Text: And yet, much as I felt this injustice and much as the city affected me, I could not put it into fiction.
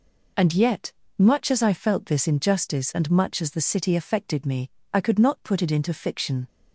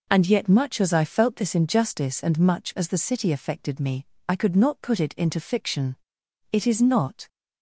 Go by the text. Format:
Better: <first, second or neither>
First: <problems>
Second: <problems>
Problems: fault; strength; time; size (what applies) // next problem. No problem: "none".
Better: first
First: none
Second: goes on to say "It is not"; noticeable; from 6.5 s on; 0.76 s long